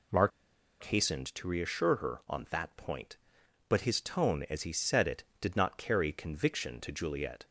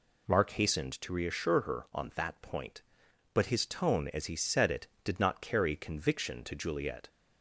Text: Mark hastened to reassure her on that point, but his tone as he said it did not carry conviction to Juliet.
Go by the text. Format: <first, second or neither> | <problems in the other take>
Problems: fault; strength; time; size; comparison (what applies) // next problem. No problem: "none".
second | pauses between "Mark" and "hastened"; noticeable; at 0.3 s; 0.54 s long